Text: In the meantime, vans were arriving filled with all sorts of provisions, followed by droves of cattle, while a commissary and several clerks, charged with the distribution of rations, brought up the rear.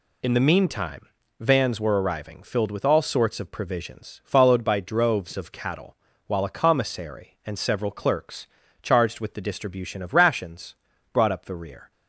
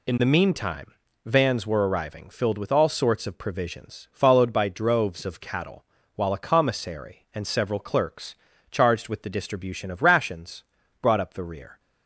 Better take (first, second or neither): neither